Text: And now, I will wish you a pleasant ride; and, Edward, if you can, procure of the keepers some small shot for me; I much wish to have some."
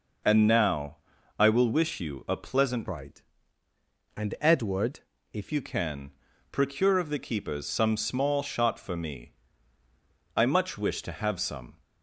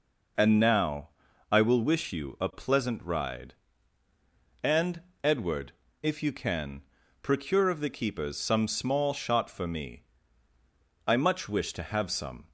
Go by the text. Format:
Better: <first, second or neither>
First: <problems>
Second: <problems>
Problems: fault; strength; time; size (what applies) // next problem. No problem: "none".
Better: second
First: changes voice from "ride" to "if"; from 2.8 to 5.5 s; 2.7 s long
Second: none